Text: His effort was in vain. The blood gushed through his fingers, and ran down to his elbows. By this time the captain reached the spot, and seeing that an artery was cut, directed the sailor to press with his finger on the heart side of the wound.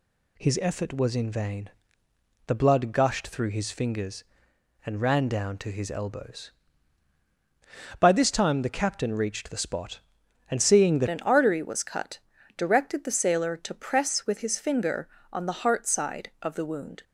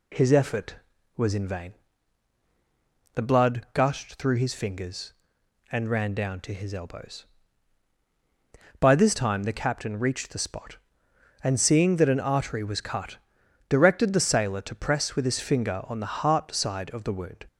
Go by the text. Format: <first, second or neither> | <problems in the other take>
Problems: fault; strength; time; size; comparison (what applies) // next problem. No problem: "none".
second | changes voice at "an"; from 11.0 s on; 6.0 s long